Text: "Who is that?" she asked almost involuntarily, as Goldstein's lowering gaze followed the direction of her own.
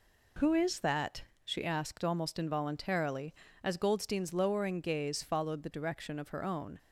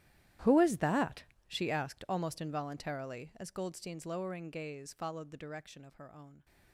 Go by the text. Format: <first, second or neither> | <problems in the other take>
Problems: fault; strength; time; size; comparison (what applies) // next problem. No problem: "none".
first | gets quieter; strong; throughout; 20 dB